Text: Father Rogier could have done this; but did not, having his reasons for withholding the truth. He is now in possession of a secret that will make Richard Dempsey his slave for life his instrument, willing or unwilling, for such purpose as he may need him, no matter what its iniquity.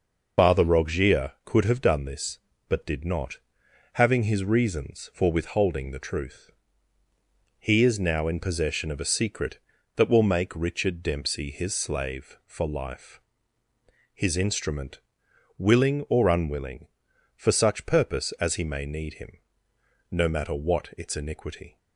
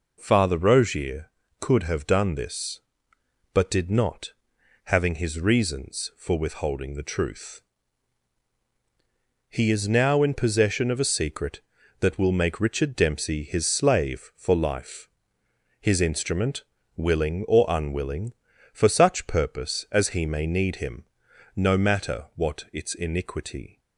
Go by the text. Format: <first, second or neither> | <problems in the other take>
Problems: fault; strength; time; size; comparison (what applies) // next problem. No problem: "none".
second | loses the start of "Father"; at 0.3 s; 50 ms // pauses between "life" and "his"; noticeable; at 13.1 s; 0.92 s long; noticeable in the second